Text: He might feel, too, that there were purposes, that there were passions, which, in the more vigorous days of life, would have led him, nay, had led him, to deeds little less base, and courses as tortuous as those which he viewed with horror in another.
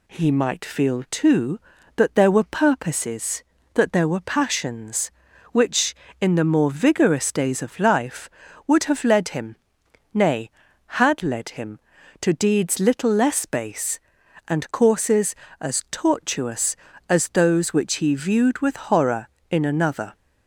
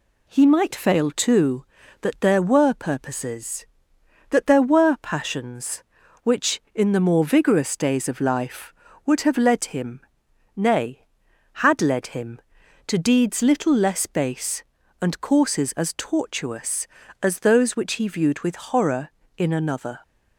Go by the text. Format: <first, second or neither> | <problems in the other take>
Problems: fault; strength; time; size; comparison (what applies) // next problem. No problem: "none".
first | says "fail" for "feel"; at 0.7 s